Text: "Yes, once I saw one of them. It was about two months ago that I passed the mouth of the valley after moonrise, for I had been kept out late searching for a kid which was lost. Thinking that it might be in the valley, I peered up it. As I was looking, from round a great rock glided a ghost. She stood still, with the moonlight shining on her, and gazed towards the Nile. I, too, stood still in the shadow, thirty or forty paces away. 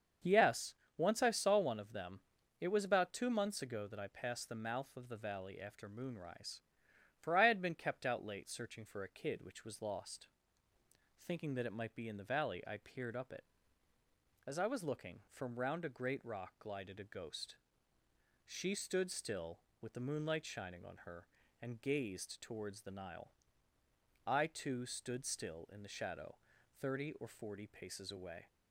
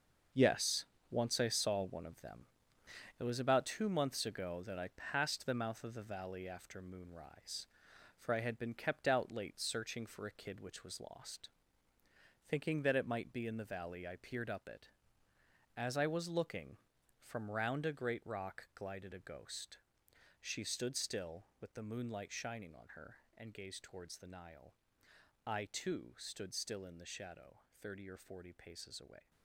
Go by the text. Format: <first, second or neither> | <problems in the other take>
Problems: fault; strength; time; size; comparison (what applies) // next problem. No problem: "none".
first | gets quieter; strong; throughout; 9.5 dB // starts louder than the rest; until 1.5 s; 6.5 dB; also in the first